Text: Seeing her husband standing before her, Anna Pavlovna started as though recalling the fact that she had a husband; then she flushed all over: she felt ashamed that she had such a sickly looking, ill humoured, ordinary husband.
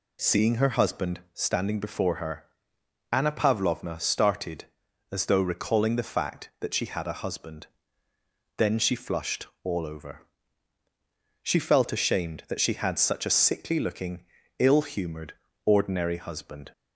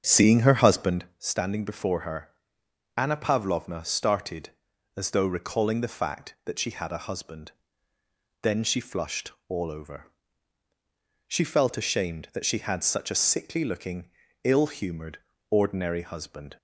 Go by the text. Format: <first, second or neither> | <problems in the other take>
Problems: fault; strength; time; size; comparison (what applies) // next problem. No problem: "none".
first | starts louder than the rest; strong; until 1.1 s; 7.5 dB // pauses between "flushed" and "all"; slight; at 9.3 s; 0.18 s long; slight in the first